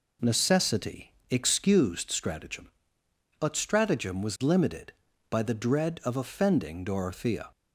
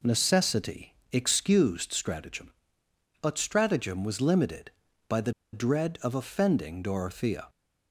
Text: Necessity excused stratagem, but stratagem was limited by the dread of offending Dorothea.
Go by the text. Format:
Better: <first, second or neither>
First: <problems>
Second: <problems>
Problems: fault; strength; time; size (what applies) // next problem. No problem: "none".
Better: first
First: pauses between "Necessity" and "excused"; slight; at 1.1 s; 0.16 s long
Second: pauses between "Necessity" and "excused"; slight; at 0.9 s; 0.16 s long // pauses between "the" and "dread"; slight; at 5.3 s; 0.22 s long